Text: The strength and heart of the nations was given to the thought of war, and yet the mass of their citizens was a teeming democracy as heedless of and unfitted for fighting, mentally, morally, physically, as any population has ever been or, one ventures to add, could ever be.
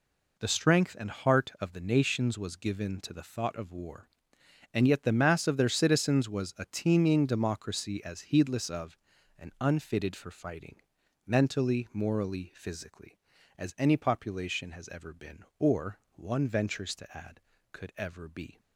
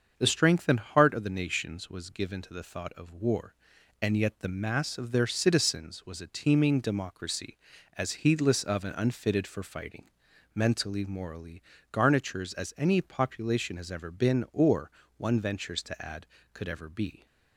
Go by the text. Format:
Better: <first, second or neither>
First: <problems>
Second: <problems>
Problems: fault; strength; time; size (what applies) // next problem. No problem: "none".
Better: first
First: none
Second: starts louder than the rest; until 1.1 s; 7 dB // says "garnitures" for "physically"; at 11.9 s